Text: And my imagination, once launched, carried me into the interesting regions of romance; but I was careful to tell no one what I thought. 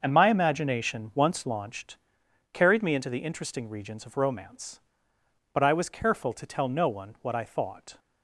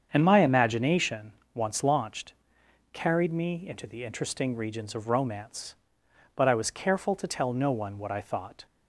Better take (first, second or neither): neither